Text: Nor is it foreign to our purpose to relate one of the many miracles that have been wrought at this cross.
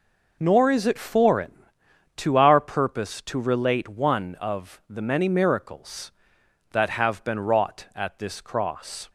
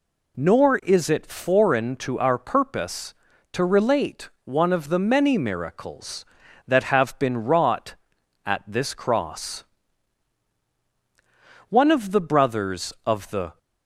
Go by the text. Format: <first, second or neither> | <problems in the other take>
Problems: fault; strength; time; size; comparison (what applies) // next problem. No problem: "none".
first | goes on to say "One of the brothers of the"; strong; from 11.6 s on; 1.8 s long